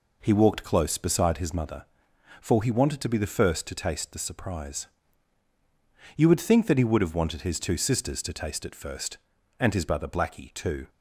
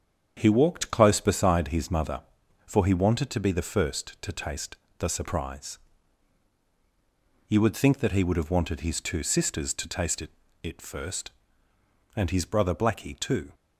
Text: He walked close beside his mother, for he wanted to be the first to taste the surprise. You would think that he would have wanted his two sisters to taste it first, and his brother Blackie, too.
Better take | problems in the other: first | starts louder than the rest; strong; until 1.3 s; 8 dB // pauses between "taste" and "the"; slight; at 4.7 s; 0.22 s long // says "it" twice; at 10.6 s

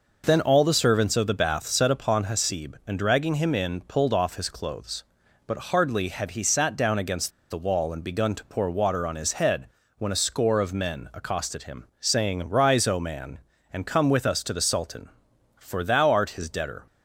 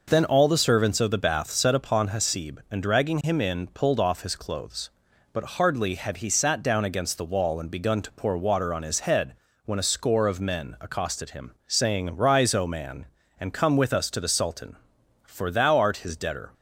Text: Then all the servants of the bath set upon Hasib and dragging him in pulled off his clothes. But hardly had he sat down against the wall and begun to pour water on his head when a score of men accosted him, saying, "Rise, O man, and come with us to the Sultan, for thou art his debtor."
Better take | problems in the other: second | pauses between "against" and "the"; slight; at 7.3 s; 0.19 s long // pauses between "head" and "when"; slight; at 9.6 s; 0.28 s long; slight in the second

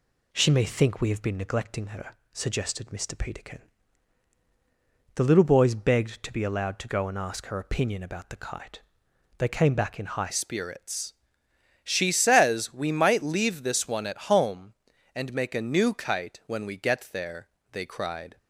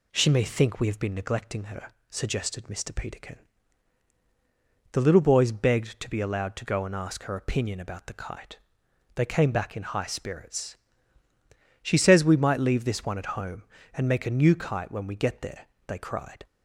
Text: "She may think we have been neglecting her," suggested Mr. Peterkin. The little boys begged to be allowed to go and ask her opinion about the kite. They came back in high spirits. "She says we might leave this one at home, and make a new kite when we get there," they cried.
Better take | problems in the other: second | changes voice at "spirits"; from 10.3 s on; 8.0 s long

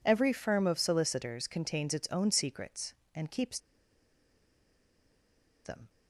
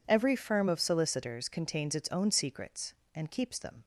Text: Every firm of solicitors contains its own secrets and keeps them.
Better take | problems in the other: second | pauses between "keeps" and "them"; strong; at 3.5 s; 2.0 s long

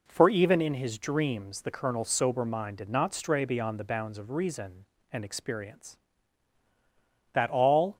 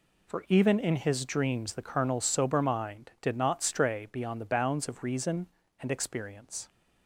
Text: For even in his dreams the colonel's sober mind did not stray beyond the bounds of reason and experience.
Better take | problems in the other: second | goes on to say "That all"; noticeable; from 7.3 s on; 0.64 s long

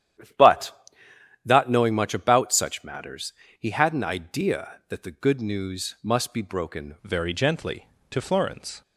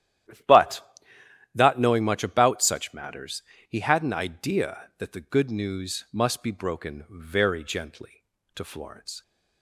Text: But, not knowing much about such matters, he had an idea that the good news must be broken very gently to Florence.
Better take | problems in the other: second | starts louder than the rest; strong; until 2.1 s; 10.5 dB; strong in the second // changes voice at "very"; from 7.0 s on; 1.8 s long

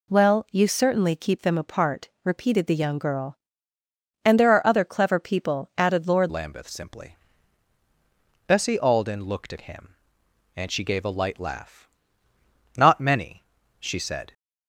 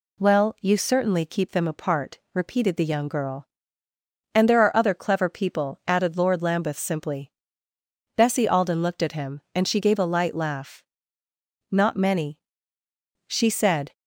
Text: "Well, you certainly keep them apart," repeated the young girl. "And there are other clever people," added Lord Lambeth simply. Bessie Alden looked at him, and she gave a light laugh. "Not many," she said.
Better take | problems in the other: second | changes voice at "Lambeth"; from 6.2 s on; 8.1 s long

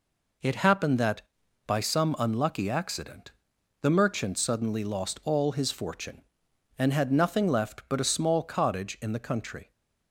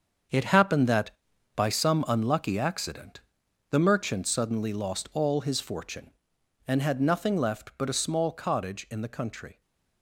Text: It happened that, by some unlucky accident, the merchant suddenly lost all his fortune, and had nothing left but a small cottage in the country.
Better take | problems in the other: first | gets quieter; strong; throughout; 10 dB

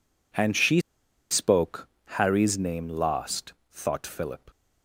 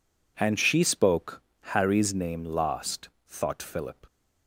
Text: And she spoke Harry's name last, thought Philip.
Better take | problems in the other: second | pauses between "she" and "spoke"; noticeable; at 0.7 s; 0.50 s long // pauses between "spoke" and "Harry's"; slight; at 1.8 s; 0.18 s long; slight in the second

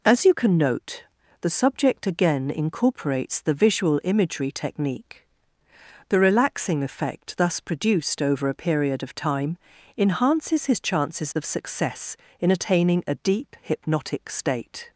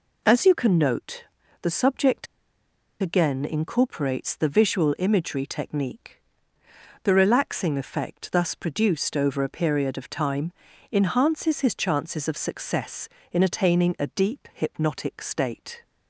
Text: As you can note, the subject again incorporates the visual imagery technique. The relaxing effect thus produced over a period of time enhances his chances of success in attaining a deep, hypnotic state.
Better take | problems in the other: first | pauses between "subject" and "again"; noticeable; at 2.2 s; 0.76 s long // pauses between "time" and "enhances"; at 10.5 s; 0.38 s long; also in the first

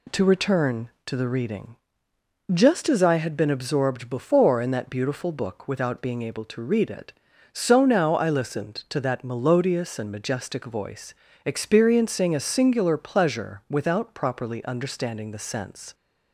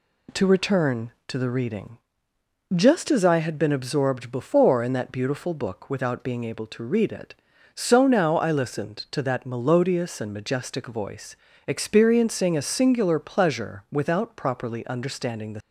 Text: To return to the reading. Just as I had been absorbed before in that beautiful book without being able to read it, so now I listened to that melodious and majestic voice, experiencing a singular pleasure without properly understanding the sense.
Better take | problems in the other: first | stops before "sense"; at 15.5 s

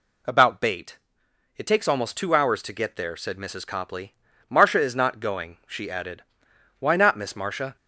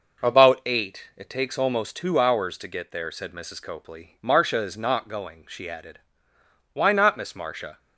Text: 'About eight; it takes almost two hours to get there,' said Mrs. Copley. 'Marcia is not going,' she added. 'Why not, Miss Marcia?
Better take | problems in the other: second | says "bait" for "eight"; at 0.6 s

